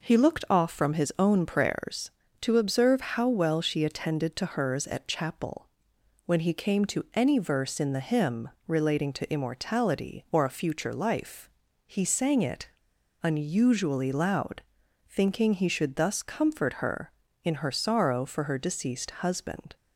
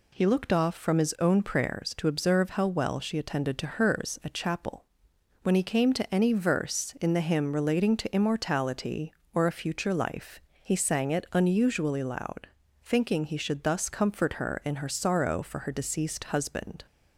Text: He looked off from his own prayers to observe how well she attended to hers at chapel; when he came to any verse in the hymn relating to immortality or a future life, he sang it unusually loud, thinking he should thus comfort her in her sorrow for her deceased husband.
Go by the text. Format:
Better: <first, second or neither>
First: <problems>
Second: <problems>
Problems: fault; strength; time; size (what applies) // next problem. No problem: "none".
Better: second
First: pauses between "hymn" and "relating"; slight; at 8.4 s; 0.16 s long // pauses between "it" and "unusually"; noticeable; at 12.6 s; 0.54 s long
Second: none